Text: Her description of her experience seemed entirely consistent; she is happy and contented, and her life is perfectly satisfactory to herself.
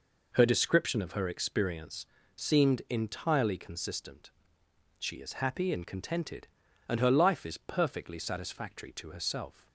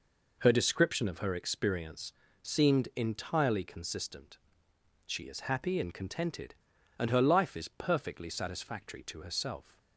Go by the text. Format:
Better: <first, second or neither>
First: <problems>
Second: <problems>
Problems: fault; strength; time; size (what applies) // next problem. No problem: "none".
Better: neither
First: pauses between "experience" and "seemed"; slight; at 2.0 s; 0.30 s long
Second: pauses between "experience" and "seemed"; slight; at 2.1 s; 0.30 s long